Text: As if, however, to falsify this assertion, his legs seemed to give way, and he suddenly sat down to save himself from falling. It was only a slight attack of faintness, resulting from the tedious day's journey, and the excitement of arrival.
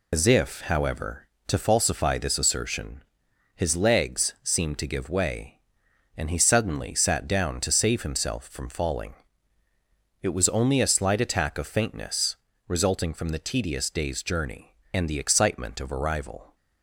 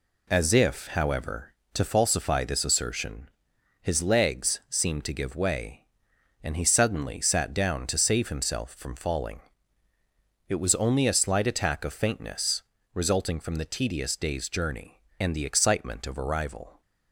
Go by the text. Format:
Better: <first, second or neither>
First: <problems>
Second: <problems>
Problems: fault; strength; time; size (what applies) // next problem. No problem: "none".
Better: second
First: loses the start of "As"; at 0.1 s; 95 ms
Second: none